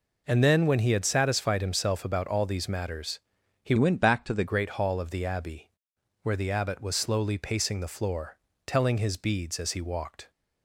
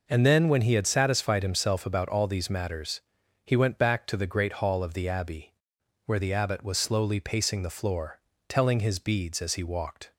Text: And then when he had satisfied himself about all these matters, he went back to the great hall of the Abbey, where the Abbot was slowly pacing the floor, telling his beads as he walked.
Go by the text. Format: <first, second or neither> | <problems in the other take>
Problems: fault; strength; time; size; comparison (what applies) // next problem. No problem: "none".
second | changes voice from "went" to "the"; from 3.7 to 4.4 s; 0.7 s long